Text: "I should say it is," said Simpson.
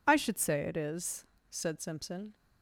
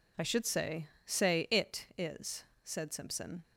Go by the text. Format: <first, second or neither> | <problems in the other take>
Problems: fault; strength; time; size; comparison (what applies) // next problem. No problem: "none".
first | says "say" twice; at 1.0 s